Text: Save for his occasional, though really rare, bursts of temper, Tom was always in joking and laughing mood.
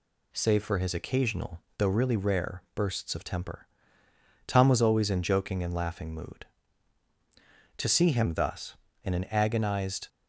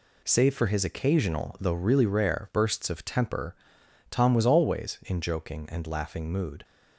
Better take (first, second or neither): second